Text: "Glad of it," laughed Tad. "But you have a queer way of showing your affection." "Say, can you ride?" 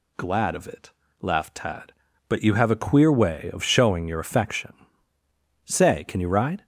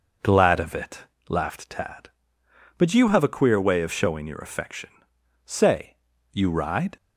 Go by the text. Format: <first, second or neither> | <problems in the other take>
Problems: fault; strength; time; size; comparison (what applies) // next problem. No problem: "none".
first | skips "can"; at 6.1 s